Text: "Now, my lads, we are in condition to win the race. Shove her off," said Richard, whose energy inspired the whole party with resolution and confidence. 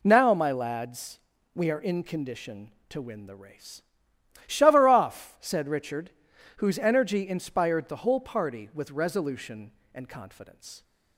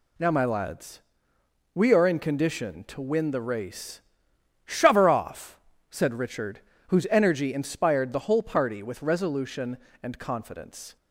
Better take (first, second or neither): neither